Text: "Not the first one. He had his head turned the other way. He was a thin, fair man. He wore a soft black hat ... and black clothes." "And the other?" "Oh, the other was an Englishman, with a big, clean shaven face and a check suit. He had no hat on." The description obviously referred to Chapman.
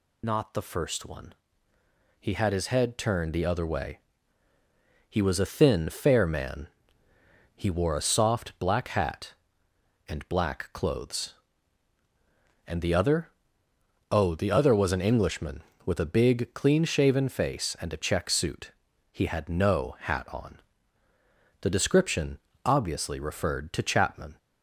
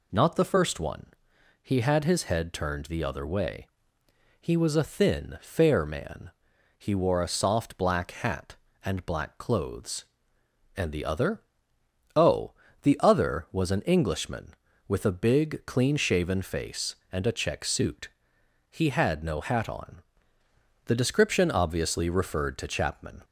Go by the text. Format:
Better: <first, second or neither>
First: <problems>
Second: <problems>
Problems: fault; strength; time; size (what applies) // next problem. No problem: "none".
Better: second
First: loses the start of "Not"; at 0.2 s; 45 ms // pauses between "description" and "obviously"; slight; at 22.3 s; 0.28 s long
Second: none